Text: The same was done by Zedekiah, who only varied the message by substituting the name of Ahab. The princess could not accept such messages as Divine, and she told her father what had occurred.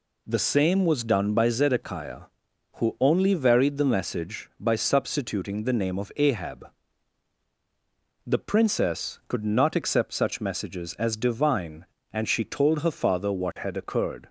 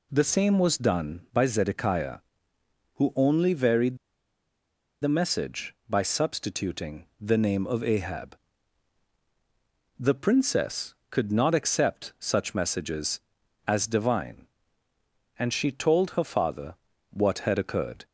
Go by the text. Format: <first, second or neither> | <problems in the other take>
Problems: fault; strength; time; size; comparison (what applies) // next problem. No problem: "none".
first | pauses between "varied" and "the"; at 3.9 s; 1.0 s long // pauses between "substituting" and "the"; slight; at 7.0 s; 0.16 s long // pauses between "father" and "what"; at 16.7 s; 0.38 s long